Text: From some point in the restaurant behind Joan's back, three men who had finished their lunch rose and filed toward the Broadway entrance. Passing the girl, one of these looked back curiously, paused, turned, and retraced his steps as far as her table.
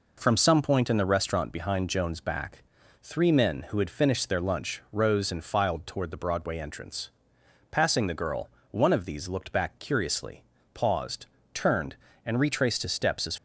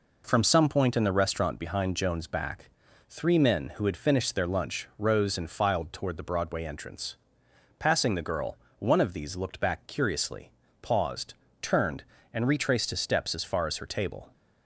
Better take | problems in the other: second | stops before "far as her table"; at 13.3 s

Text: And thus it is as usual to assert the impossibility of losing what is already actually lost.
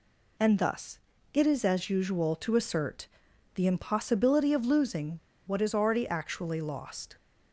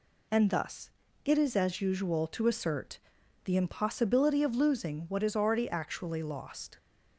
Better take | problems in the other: second | pauses between "thus" and "it"; slight; at 0.9 s; 0.34 s long; slight in the second // pauses between "assert" and "the"; noticeable; at 3.0 s; 0.48 s long; noticeable in the second // pauses between "losing" and "what"; slight; at 5.1 s; 0.30 s long

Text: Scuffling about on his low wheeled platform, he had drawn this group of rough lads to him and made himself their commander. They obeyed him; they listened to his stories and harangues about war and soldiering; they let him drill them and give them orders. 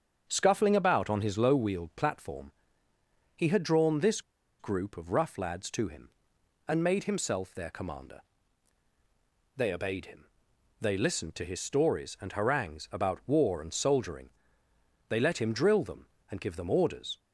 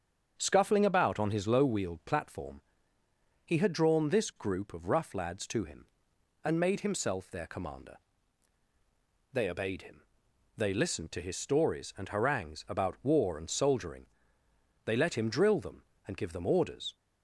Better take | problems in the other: second | starts louder than the rest; strong; until 1.2 s; 7 dB; strong in the second // pauses between "this" and "group"; at 4.2 s; 0.38 s long

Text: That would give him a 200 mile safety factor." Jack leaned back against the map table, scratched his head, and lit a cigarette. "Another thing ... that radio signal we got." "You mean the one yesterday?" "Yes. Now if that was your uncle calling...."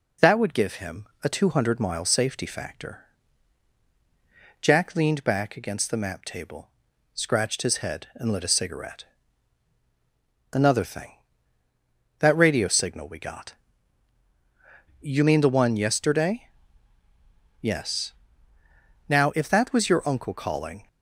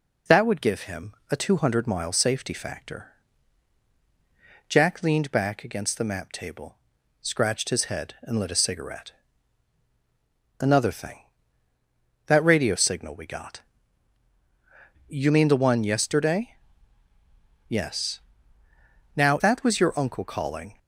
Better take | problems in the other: first | pauses between "him" and "a"; slight; at 1.1 s; 0.16 s long; slight in the first // skips "if"; at 19.3 s

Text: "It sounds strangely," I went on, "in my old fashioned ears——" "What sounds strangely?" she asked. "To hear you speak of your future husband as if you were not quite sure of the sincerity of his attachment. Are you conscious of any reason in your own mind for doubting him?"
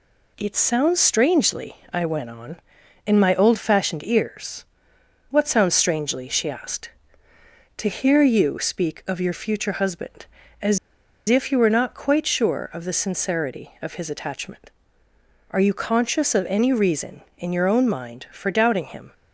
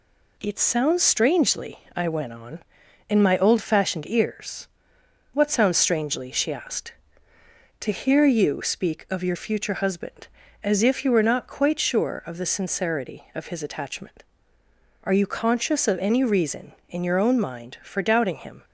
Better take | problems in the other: second | pauses between "as" and "if"; noticeable; at 10.7 s; 0.50 s long

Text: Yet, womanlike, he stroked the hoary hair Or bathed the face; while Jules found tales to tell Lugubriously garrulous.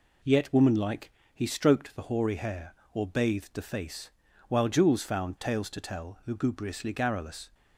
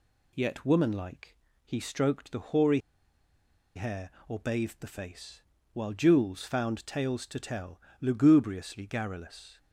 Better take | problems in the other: first | pauses between "hoary" and "hair"; noticeable; at 2.8 s; 0.95 s long // pauses between "tell" and "Lugubriously"; slight; at 7.8 s; 0.18 s long

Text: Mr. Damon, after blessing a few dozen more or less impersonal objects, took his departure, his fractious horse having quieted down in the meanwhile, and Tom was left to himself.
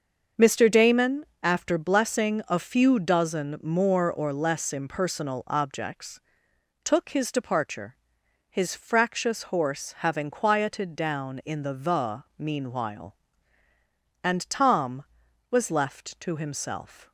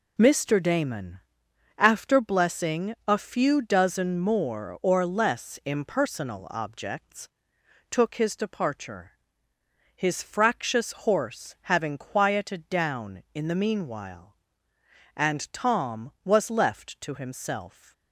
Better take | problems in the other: second | starts louder than the rest; until 1.5 s; 6.5 dB // says "the" twice; at 11.7 s

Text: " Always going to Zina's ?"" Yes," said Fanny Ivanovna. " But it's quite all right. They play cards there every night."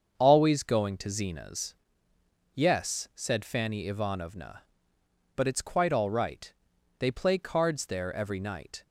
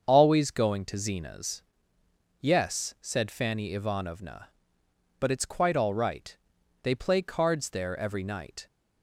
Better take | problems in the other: neither | starts louder than the rest; strong; the same in both

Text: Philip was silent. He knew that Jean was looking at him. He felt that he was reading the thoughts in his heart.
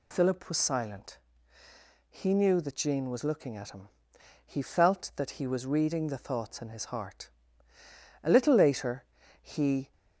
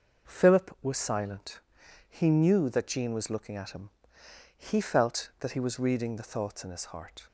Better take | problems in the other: second | goes on to say "A little later he"; from 8.2 s on; 1.6 s long

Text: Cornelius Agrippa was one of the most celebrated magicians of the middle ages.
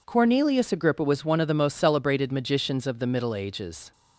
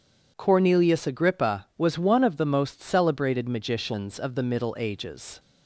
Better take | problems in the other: neither | none

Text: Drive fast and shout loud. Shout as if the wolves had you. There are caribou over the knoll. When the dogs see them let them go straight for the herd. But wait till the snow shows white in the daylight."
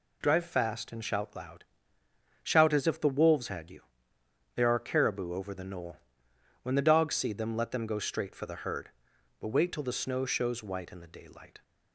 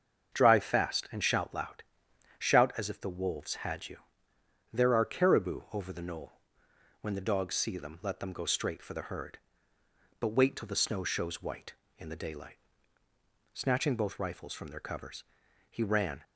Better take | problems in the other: first | starts louder than the rest; until 1.3 s; 7 dB // goes on to say "Snatching both rifles from their covers he ran"; strong; from 13.5 s on; 2.7 s long

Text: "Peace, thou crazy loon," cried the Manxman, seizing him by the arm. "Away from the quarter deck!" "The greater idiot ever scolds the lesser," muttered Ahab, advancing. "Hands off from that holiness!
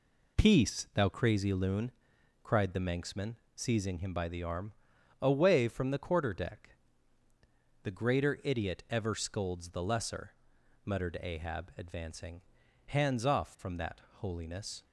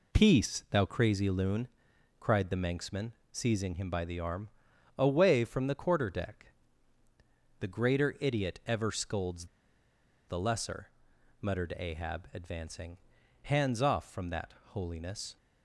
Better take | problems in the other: first | pauses between "scolds" and "the"; noticeable; at 9.4 s; 0.82 s long // pauses between "that" and "holiness"; slight; at 14.5 s; 0.18 s long; slight in the first

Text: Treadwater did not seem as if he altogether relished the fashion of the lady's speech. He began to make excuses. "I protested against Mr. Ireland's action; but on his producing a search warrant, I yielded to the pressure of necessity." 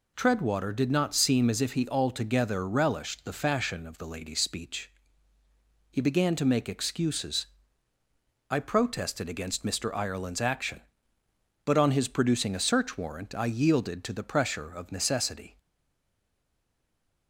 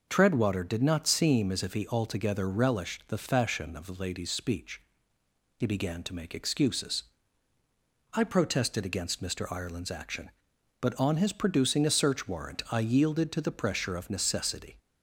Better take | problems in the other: second | stays silent after the last word; noticeable; from 15.5 s on; 1.7 s long

